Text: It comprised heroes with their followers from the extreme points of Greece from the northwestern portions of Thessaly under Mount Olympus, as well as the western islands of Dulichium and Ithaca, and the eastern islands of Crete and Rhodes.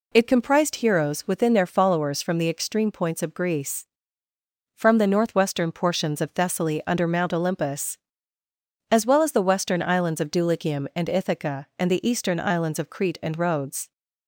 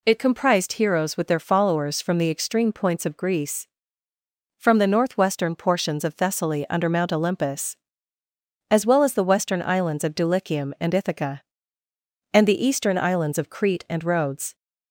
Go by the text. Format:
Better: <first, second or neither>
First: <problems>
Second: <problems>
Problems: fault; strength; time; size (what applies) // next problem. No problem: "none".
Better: second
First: says "within" for "with"; at 1.2 s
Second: none